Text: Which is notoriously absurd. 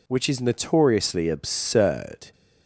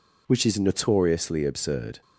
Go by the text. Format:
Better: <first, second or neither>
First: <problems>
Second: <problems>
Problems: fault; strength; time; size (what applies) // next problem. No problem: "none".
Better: neither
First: none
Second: none